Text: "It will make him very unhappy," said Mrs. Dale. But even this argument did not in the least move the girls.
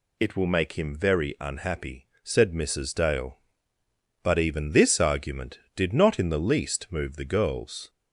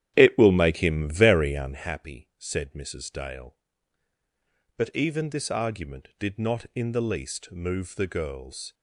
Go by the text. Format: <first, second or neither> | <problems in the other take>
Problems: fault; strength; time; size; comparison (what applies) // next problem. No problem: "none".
first | starts louder than the rest; strong; until 1.9 s; 11 dB